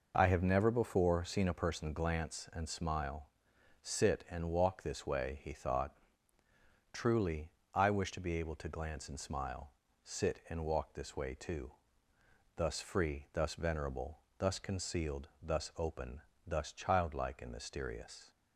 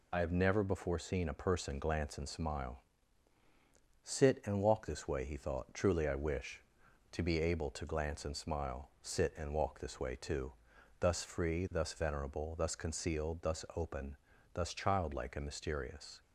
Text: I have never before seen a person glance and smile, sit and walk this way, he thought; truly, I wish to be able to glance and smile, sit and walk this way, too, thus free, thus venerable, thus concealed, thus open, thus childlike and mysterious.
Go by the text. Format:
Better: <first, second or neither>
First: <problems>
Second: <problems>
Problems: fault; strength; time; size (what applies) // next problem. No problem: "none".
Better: first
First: none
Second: loses the start of "I"; at 0.1 s; 50 ms